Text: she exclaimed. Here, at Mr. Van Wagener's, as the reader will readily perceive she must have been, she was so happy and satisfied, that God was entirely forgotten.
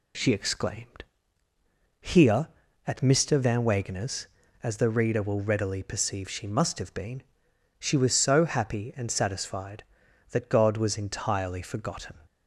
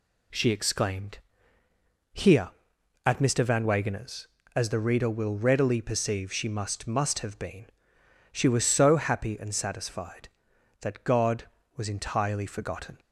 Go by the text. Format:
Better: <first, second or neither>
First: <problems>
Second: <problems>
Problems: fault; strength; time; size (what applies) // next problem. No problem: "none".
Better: first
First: none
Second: says "must" twice; at 6.8 s